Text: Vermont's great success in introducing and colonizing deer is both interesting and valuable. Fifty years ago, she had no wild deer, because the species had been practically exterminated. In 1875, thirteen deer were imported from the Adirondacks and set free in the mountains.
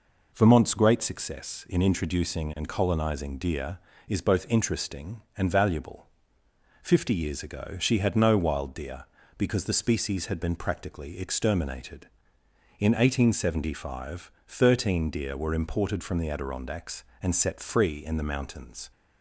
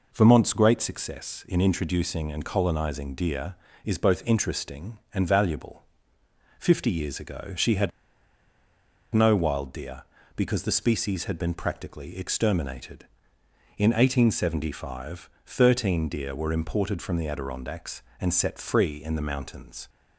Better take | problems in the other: first | pauses between "had" and "no"; at 7.9 s; 1.2 s long

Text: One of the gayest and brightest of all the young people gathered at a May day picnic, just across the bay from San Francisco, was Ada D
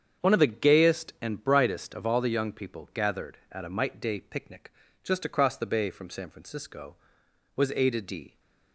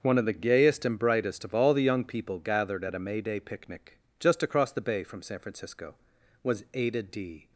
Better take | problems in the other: second | starts louder than the rest; strong; until 1.3 s; 7.5 dB; also in the second // says "Might" for "May"; at 3.6 s

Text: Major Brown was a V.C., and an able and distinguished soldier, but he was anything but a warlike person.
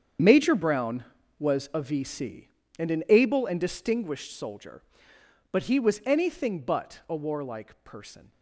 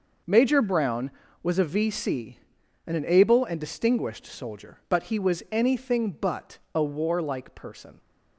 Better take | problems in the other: second | gets quieter; strong; throughout; 14 dB

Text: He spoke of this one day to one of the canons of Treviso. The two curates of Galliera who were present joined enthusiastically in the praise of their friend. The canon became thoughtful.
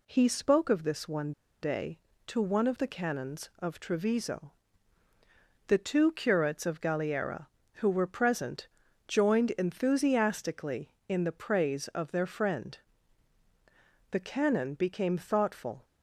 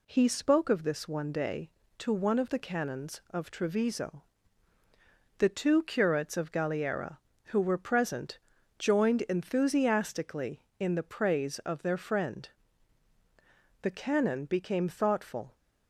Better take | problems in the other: second | pauses between "one" and "day"; slight; at 1.3 s; 0.31 s long // pauses between "present" and "joined"; at 8.6 s; 0.40 s long; also in the second

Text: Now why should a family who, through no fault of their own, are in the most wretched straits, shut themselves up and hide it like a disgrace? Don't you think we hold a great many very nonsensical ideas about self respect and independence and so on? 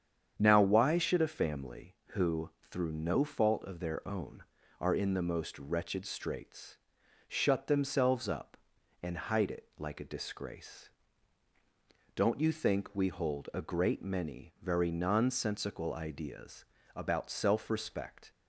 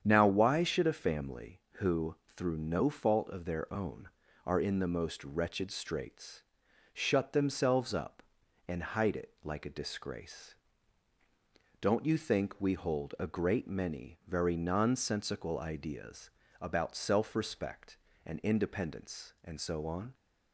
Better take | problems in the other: second | starts louder than the rest; strong; until 1.3 s; 8 dB; strong in the second // pauses between "ideas" and "about"; slight; at 16.6 s; 0.30 s long; slight in the second // stops before "and independence and so on"; at 18.3 s

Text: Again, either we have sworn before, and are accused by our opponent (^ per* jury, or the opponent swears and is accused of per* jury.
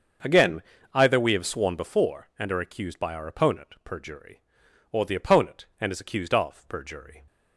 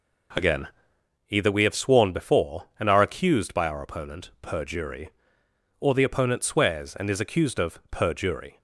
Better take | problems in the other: second | starts louder than the rest; until 1.5 s; 6.5 dB // skips "swears"; at 5.7 s

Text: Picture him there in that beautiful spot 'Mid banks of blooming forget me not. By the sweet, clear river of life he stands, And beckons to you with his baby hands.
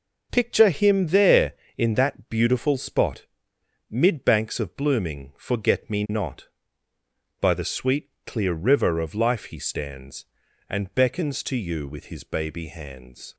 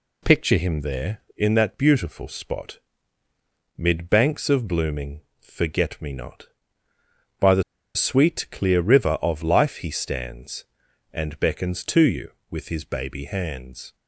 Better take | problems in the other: first | pauses between "spot" and "Mid"; noticeable; at 2.7 s; 0.98 s long; noticeable in the first // pauses between "blooming" and "forget"; slight; at 5.2 s; 0.20 s long // pauses between "the" and "sweet"; slight; at 7.6 s; 0.33 s long

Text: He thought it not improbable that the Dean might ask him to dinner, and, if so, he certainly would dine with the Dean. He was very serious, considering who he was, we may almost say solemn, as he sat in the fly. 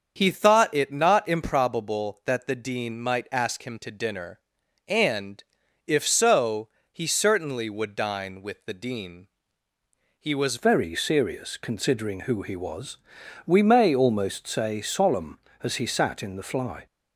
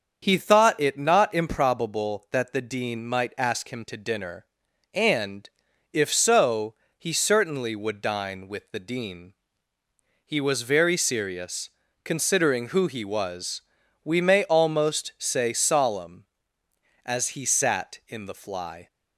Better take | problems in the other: second | starts louder than the rest; until 1.2 s; 7 dB; also in the second // changes voice at "very"; from 10.5 s on; 6.3 s long

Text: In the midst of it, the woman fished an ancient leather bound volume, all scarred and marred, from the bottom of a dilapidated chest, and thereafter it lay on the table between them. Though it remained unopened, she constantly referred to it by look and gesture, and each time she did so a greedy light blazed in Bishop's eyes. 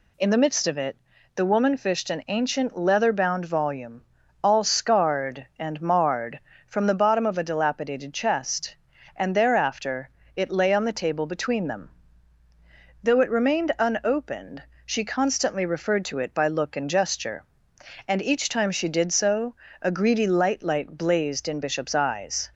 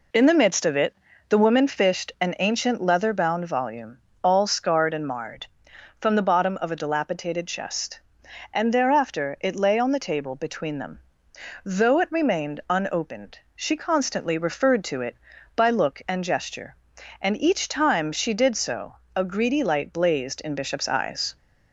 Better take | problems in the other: second | pauses between "thereafter" and "it"; slight; at 10.0 s; 0.28 s long // pauses between "so" and "a"; slight; at 19.5 s; 0.26 s long; slight in the second // says "light" twice; at 20.6 s

